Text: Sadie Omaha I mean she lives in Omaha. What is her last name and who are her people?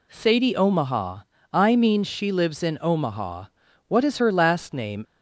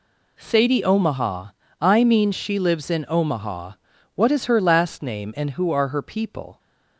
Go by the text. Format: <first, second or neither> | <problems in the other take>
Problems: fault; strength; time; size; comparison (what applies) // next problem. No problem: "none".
second | pauses between "Omaha" and "I"; slight; at 1.2 s; 0.28 s long; slight in the second // stops before "and who are her people"; at 5.0 s